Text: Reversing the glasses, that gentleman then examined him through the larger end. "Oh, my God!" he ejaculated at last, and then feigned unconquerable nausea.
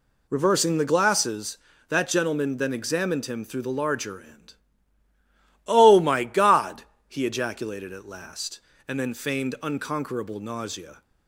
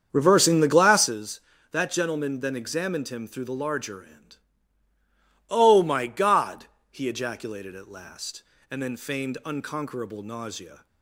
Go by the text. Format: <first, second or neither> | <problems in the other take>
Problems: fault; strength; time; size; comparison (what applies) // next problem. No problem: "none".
first | starts louder than the rest; strong; until 1.1 s; 7.5 dB